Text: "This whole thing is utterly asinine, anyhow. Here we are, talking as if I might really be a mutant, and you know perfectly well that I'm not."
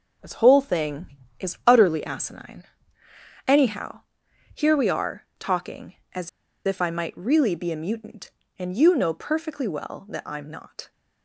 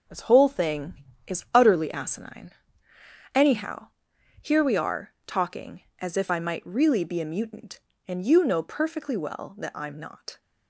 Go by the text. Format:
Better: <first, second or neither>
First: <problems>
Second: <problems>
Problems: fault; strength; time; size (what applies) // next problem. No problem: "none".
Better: second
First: pauses between "as" and "if"; slight; at 6.2 s; 0.36 s long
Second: none